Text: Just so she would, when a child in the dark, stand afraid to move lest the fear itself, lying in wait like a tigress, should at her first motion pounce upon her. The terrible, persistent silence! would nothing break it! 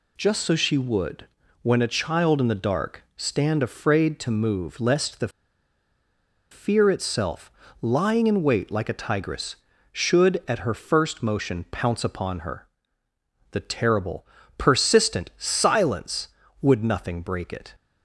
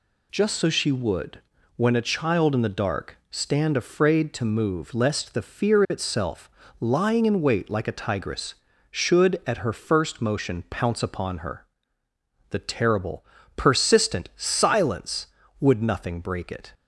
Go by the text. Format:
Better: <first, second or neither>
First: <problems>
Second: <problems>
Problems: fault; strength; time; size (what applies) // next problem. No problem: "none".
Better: second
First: pauses between "the" and "fear"; at 5.2 s; 1.2 s long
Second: none